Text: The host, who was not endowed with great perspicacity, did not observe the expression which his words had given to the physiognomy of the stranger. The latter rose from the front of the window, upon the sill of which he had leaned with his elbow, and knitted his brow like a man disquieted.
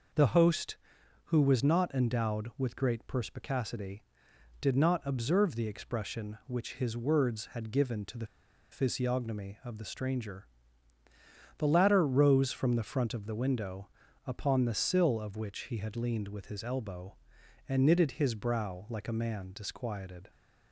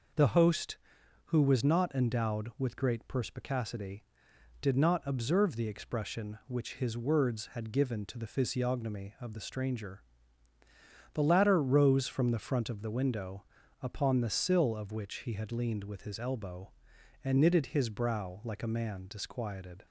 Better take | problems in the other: second | pauses between "the" and "physiognomy"; at 8.2 s; 0.45 s long

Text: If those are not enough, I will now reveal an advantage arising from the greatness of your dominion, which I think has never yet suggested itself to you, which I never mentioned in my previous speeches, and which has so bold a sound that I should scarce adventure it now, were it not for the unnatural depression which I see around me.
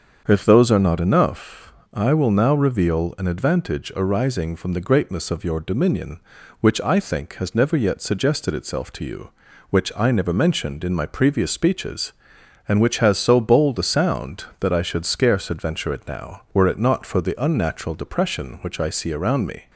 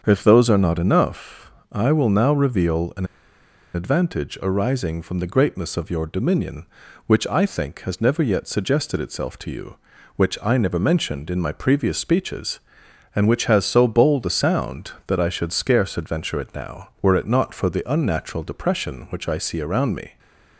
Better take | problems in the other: first | starts louder than the rest; until 1.0 s; 7 dB; also in the first // pauses between "an" and "advantage"; noticeable; at 3.0 s; 0.69 s long // stays silent after the last word; slight; from 20.0 s on; 0.5 s long

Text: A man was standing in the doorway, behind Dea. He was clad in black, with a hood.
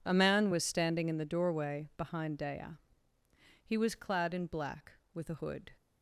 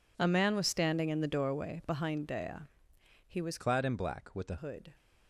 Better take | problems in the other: first | changes voice from "clad" to "a"; from 3.5 to 4.5 s; 1.0 s long

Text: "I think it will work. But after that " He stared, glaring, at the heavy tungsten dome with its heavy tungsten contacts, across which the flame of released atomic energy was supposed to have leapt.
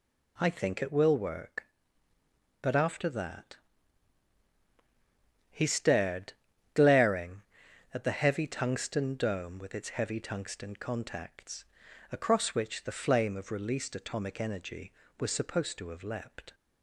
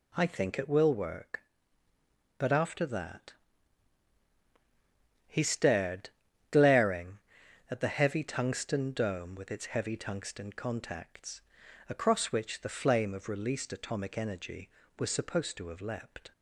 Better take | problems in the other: neither | none

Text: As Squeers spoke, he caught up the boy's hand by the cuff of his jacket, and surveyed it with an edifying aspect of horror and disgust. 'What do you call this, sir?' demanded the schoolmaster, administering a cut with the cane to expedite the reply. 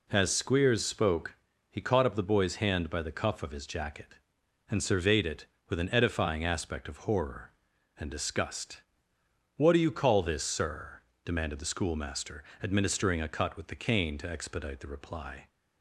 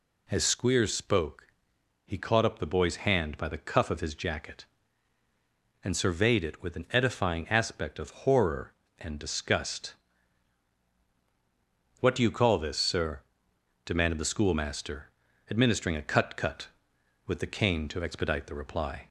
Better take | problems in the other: first | says "cut" twice; at 16.3 s

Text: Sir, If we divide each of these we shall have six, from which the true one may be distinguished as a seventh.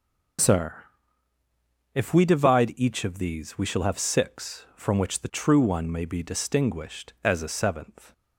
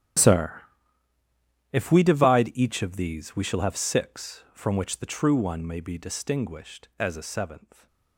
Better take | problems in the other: first | gets quieter; strong; throughout; 21 dB // starts louder than the rest; strong; until 2.4 s; 11.5 dB; also in the first

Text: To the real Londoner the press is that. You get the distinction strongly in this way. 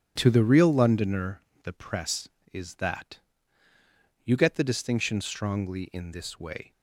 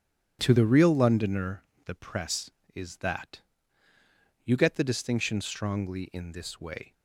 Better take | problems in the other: neither | starts louder than the rest; strong; the same in both // pauses between "Londoner" and "the"; slight; the same in both

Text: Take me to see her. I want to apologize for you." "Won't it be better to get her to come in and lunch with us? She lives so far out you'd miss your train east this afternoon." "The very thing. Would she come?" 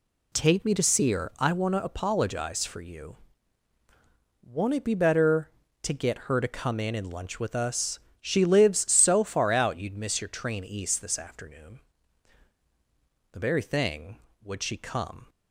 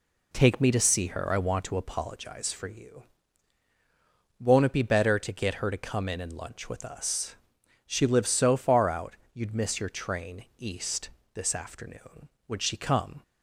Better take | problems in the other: first | pauses between "out" and "you'd"; slight; at 9.1 s; 0.20 s long // pauses between "east" and "this"; slight; at 11.1 s; 0.24 s long // skips "The very thing"; at 12.3 s

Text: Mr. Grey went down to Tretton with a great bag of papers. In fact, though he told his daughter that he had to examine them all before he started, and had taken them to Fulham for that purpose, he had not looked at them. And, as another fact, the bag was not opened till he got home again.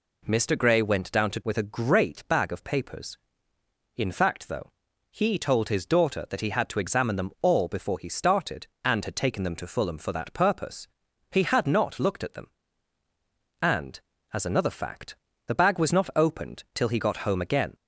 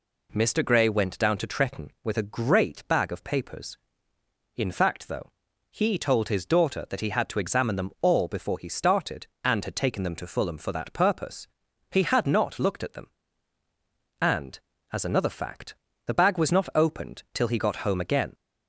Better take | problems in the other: second | skips "Tretton"; at 1.4 s // pauses between "though" and "he"; at 4.7 s; 0.42 s long; also in the second

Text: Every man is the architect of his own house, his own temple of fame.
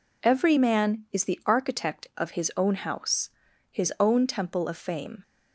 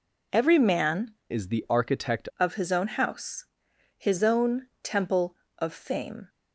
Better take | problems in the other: first | changes voice from "is" to "architect"; from 1.3 to 2.2 s; 0.9 s long // pauses between "own" and "temple"; slight; at 4.6 s; 0.16 s long

